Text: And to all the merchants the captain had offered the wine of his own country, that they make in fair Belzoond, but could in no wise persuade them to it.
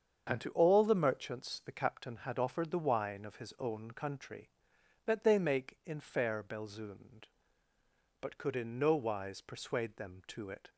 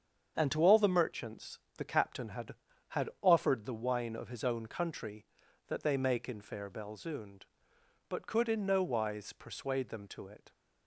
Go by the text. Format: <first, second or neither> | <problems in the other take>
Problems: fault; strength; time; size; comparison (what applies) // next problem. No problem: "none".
first | starts louder than the rest; strong; until 1.3 s; 7.5 dB; strong in the first // pauses between "merchants" and "the"; slight; at 1.5 s; 0.20 s long // says "had" twice; at 2.8 s